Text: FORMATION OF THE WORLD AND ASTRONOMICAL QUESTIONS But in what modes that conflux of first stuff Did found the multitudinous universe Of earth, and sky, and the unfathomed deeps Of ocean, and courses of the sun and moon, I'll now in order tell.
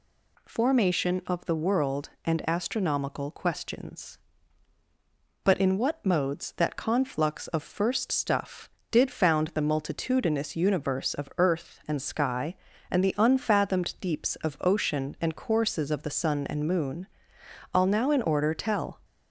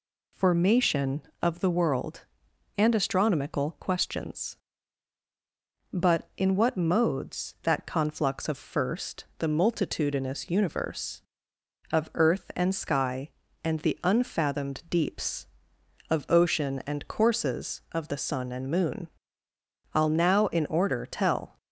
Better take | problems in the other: first | skips "stuff Did found"; at 9.3 s

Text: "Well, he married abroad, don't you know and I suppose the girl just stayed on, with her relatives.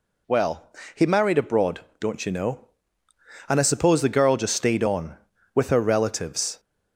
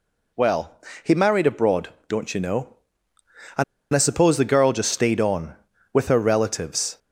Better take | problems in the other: first | pauses between "and" and "I"; slight; at 3.6 s; 0.30 s long

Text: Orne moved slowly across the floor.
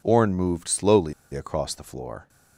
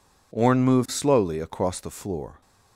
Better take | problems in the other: second | pauses between "slowly" and "across"; slight; at 1.1 s; 0.21 s long

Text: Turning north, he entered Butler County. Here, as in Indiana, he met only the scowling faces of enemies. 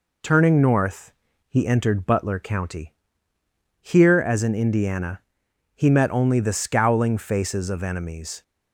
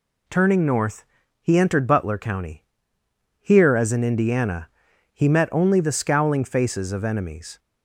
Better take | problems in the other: neither | none

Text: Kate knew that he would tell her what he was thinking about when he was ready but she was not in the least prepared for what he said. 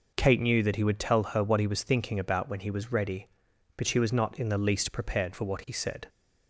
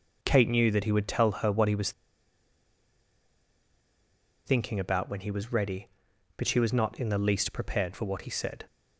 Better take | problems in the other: first | pauses between "was" and "thinking"; strong; at 1.9 s; 2.5 s long

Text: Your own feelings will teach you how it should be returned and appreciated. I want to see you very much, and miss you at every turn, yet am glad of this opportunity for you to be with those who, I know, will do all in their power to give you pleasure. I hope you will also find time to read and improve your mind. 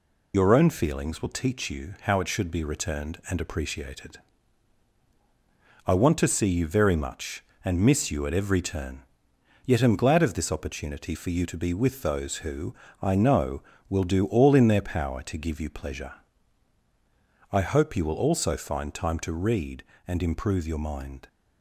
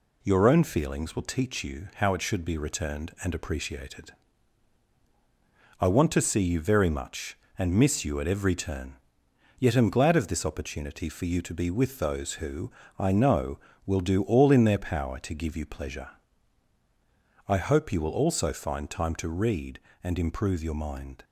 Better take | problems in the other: second | loses the start of "Your"; at 0.3 s; 55 ms

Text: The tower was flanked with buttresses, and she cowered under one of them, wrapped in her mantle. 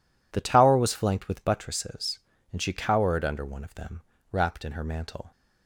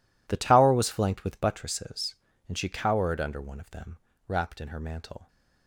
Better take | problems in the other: first | gets quieter; strong; throughout; 16 dB

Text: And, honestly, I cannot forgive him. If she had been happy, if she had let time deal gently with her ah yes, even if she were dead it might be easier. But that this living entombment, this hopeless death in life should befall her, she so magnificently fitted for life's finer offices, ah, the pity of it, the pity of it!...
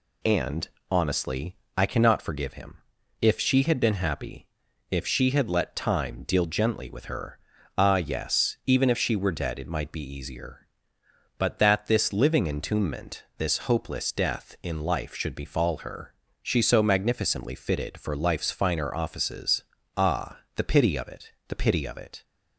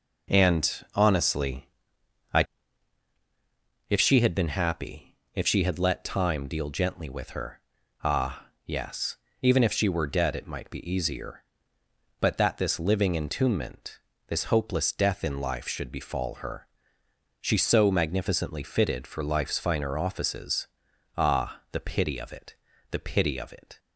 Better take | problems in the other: first | skips "cannot forgive him"; at 3.1 s // pauses between "her" and "ah"; at 7.6 s; 0.42 s long; also in the first // pauses between "ah" and "yes"; slight; at 8.4 s; 0.20 s long

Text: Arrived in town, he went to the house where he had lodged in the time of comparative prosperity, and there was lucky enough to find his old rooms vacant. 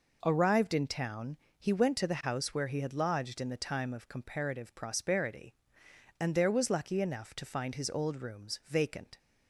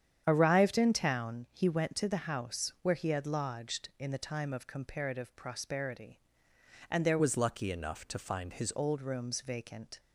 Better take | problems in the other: first | starts louder than the rest; strong; until 1.2 s; 9 dB // changes voice from "was" to "his"; from 7.1 to 8.7 s; 1.6 s long

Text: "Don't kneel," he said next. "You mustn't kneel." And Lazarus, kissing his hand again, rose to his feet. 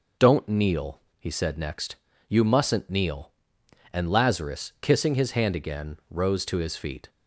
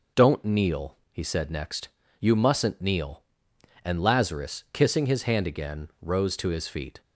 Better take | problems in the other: neither | none

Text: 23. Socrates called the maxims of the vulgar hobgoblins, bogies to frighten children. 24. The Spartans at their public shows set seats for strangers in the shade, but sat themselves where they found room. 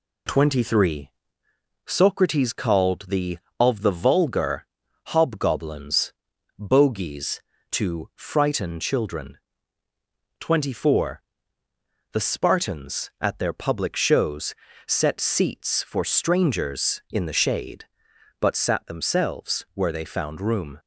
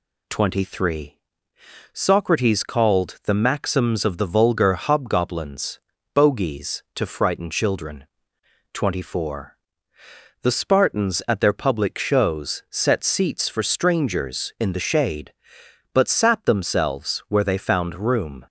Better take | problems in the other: second | skips "maxims"; at 3.4 s // pauses between "vulgar" and "hobgoblins"; at 4.6 s; 0.40 s long // pauses between "shows" and "set"; slight; at 14.5 s; 0.32 s long

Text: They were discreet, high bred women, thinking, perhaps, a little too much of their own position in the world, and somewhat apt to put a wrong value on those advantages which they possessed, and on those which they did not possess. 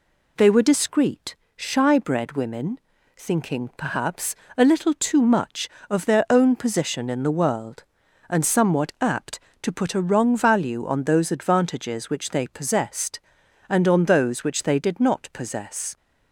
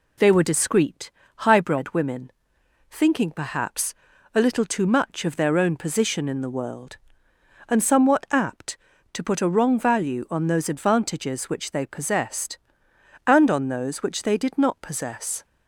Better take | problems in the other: second | says "shy" for "high"; at 1.5 s

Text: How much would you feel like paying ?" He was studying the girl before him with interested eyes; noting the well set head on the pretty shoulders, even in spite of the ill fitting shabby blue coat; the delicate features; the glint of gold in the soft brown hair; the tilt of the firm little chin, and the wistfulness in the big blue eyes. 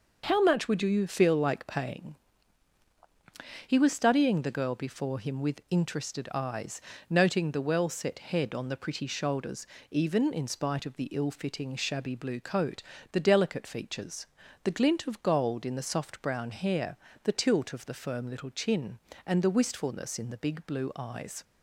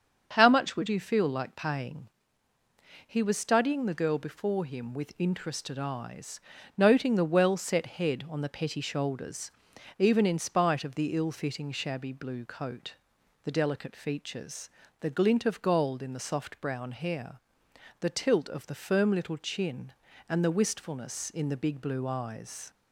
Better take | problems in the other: first | starts louder than the rest; strong; until 1.3 s; 7.5 dB // says "petty" for "pretty"; at 8.4 s

